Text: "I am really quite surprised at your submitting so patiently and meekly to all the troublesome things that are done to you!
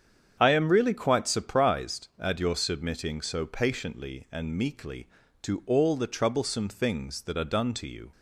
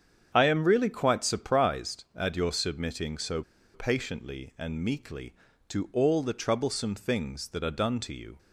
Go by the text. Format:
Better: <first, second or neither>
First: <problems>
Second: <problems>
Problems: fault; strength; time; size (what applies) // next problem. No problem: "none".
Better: first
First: starts louder than the rest; strong; until 1.4 s; 8 dB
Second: starts louder than the rest; strong; until 1.3 s; 8 dB // pauses between "so" and "patiently"; slight; at 3.4 s; 0.31 s long